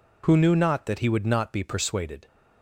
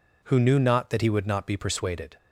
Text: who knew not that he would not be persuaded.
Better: neither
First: none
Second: none

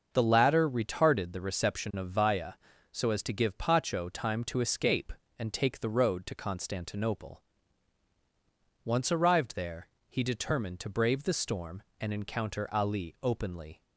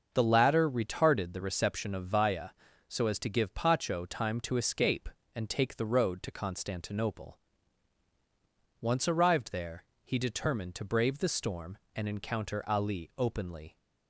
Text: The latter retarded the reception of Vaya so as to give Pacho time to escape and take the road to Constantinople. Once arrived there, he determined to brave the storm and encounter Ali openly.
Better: neither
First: starts louder than the rest; until 1.1 s; 6.5 dB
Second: starts louder than the rest; until 1.1 s; 6.5 dB

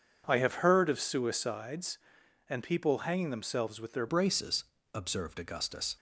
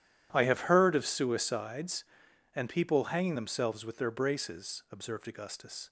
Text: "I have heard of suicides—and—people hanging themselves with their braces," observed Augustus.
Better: second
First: changes voice at "braces"; from 4.0 s on; 1.9 s long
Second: none

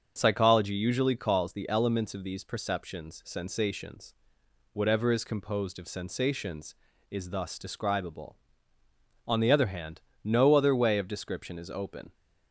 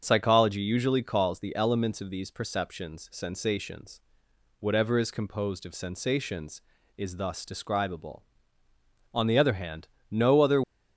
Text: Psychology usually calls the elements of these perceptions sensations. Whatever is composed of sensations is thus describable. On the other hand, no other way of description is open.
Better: first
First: starts louder than the rest; until 1.1 s; 7 dB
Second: starts louder than the rest; until 1.0 s; 7 dB // stops before "way of description is open"; at 10.6 s

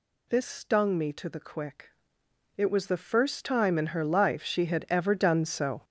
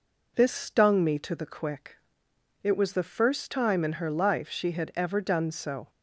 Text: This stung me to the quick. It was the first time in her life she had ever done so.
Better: second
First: gets louder; strong; throughout; 9.5 dB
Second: none

